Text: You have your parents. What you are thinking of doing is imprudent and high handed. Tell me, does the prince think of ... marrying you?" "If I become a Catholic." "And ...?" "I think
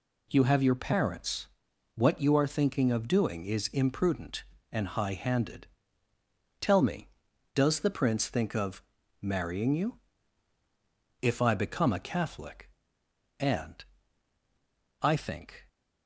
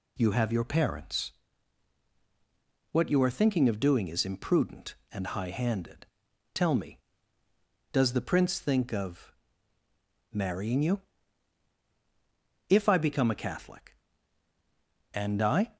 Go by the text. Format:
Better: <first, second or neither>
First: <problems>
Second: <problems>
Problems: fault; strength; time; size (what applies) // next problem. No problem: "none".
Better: first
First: none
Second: stops before "think"; at 15.7 s